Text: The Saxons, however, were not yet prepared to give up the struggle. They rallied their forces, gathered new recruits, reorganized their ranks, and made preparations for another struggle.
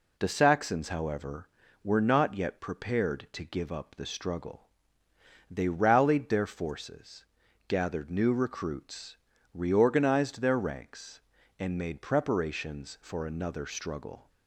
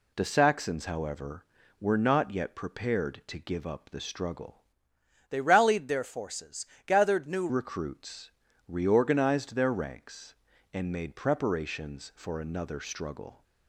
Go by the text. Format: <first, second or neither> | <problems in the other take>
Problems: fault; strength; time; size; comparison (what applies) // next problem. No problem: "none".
first | changes voice from "They" to "new"; from 5.2 to 7.4 s; 2.2 s long